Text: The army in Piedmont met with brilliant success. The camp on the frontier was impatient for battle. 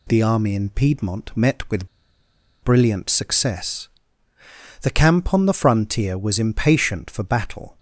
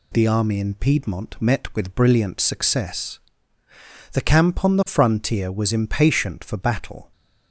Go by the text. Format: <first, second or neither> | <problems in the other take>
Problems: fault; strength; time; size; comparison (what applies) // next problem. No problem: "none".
second | pauses between "with" and "brilliant"; noticeable; at 1.8 s; 0.75 s long